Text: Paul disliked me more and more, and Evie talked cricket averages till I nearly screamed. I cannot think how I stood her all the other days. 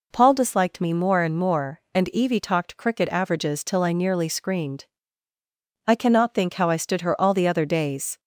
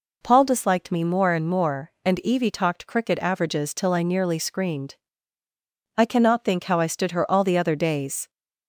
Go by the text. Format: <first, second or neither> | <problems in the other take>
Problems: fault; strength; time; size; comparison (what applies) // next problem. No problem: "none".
neither | none